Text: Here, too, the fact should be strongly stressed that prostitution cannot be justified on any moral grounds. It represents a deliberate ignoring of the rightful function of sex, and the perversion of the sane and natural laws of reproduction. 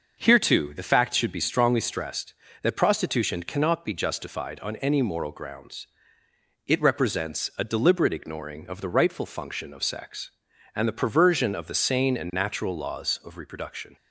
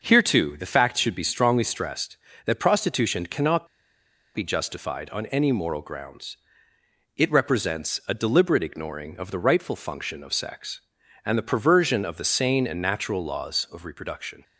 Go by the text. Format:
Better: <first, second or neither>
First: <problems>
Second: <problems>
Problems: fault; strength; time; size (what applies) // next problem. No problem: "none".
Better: first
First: starts louder than the rest; until 1.2 s; 6 dB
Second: starts louder than the rest; until 1.0 s; 6 dB // pauses between "cannot" and "be"; noticeable; at 3.6 s; 0.67 s long